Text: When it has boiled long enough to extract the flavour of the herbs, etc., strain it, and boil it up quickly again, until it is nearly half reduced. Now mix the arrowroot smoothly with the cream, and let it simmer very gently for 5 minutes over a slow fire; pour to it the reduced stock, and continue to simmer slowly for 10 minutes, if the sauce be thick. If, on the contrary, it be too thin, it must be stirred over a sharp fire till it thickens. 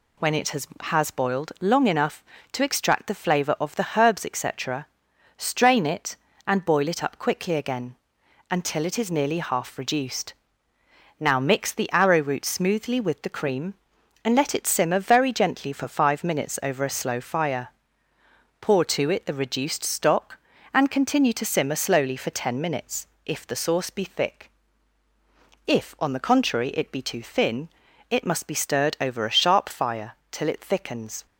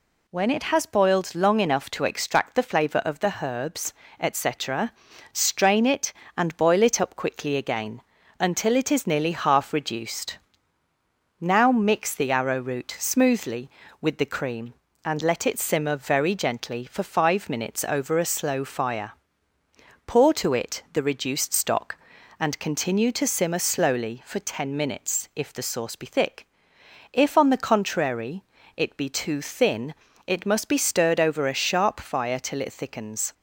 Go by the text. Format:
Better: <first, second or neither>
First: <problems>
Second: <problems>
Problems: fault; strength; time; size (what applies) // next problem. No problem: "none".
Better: second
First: says "has" twice; at 0.8 s // pauses between "fire" and "till"; slight; at 30.1 s; 0.18 s long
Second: none